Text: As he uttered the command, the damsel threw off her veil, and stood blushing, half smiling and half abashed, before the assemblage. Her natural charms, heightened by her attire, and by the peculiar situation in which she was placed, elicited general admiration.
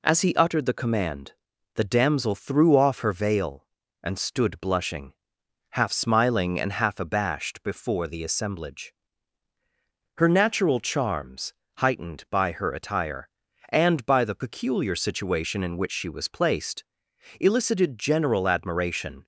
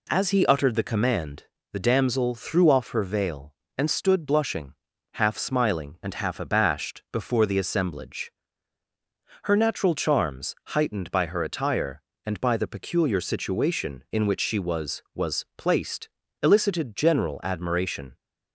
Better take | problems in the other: first | says "was" twice; at 15.1 s

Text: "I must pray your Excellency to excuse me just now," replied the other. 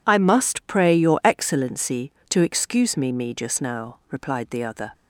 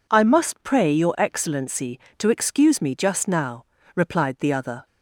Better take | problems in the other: second | says "me" twice; at 3.1 s

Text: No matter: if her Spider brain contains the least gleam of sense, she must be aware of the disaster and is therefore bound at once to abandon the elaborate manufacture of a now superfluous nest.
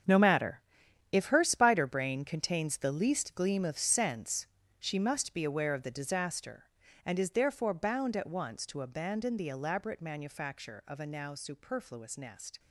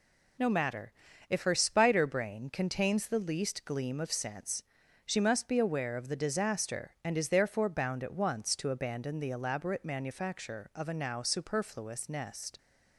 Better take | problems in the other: second | gets quieter; strong; throughout; 12.5 dB

